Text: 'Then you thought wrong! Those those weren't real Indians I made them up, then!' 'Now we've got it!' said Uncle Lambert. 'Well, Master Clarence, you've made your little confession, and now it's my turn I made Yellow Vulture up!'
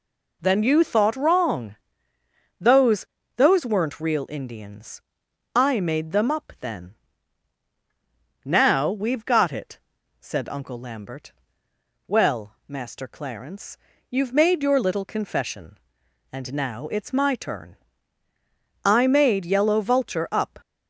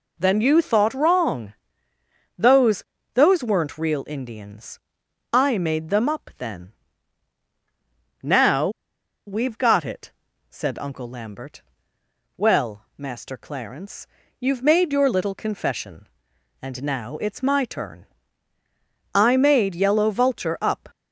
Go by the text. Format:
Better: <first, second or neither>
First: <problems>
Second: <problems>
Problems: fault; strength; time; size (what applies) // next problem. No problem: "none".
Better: first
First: pauses between "Those" and "those"; slight; at 3.0 s; 0.32 s long // pauses between "Indians" and "I"; noticeable; at 5.0 s; 0.54 s long // pauses between "turn" and "I"; at 17.7 s; 1.0 s long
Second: pauses between "Those" and "those"; slight; at 2.8 s; 0.32 s long // pauses between "Indians" and "I"; noticeable; at 4.7 s; 0.54 s long // pauses between "Now" and "we've"; noticeable; at 8.6 s; 0.57 s long // pauses between "turn" and "I"; at 18.0 s; 1.0 s long